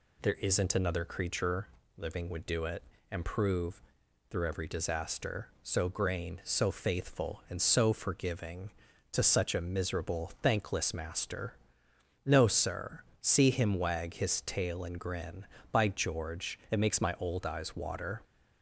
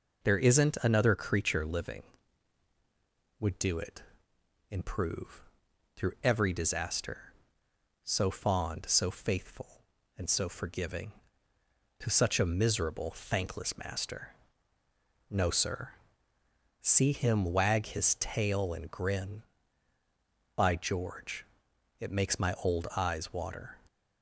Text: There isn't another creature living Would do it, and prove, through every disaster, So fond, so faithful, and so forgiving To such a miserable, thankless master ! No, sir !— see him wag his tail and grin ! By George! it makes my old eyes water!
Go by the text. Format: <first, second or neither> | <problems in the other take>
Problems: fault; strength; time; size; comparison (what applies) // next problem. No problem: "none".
second | pauses between "creature" and "living"; slight; at 1.6 s; 0.28 s long // says "grain" for "fond"; at 5.8 s